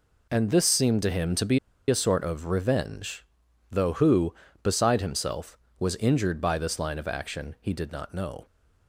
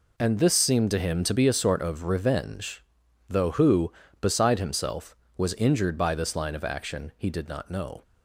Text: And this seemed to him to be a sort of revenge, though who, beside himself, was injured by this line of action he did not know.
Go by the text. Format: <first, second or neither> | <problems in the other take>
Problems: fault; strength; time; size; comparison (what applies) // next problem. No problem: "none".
second | pauses between "be" and "a"; slight; at 1.5 s; 0.30 s long